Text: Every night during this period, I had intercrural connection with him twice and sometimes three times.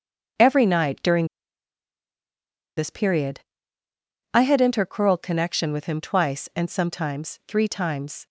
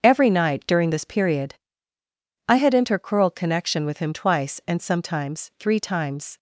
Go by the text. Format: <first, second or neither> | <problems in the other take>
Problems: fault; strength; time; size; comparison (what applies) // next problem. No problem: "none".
second | starts louder than the rest; until 2.9 s; 7 dB; also in the second // pauses between "during" and "this"; strong; at 1.2 s; 1.5 s long